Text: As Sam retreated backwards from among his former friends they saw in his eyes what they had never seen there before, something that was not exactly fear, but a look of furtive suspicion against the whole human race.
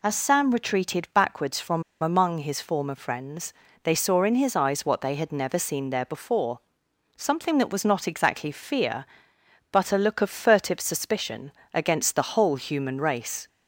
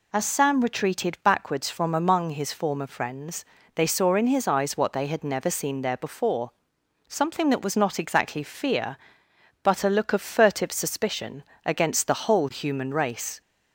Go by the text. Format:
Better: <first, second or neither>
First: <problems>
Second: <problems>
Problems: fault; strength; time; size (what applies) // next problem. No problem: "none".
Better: second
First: pauses between "from" and "among"; slight; at 1.8 s; 0.20 s long // pauses between "friends" and "they"; slight; at 3.5 s; 0.30 s long // pauses between "suspicion" and "against"; slight; at 11.5 s; 0.22 s long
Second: pauses between "friends" and "they"; slight; at 3.4 s; 0.30 s long // pauses between "suspicion" and "against"; slight; at 11.4 s; 0.22 s long